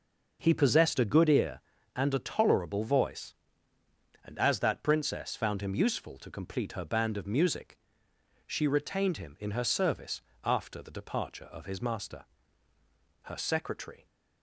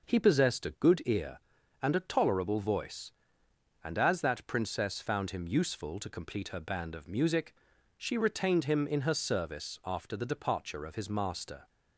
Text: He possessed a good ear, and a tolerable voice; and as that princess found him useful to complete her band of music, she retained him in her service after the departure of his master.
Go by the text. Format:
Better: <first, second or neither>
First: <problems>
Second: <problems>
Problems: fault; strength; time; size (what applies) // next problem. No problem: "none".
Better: second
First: pauses between "service" and "after"; slight; at 10.2 s; 0.20 s long // goes on to say "Her secretary"; noticeable; from 13.2 s on; 0.82 s long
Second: none